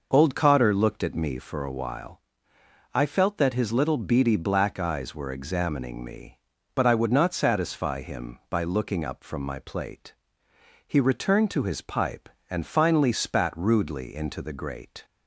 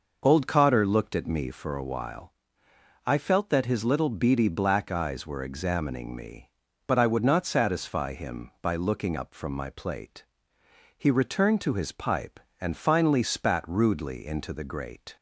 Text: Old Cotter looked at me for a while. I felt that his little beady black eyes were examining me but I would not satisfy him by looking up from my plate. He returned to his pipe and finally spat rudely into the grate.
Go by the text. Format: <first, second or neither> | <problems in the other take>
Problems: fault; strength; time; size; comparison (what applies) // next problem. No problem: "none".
neither | none